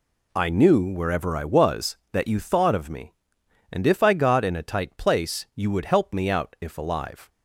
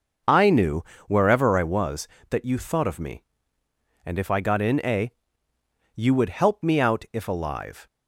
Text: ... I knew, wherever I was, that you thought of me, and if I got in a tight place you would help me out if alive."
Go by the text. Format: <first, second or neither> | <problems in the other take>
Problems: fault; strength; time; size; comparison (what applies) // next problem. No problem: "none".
first | skips "tight place"; at 5.5 s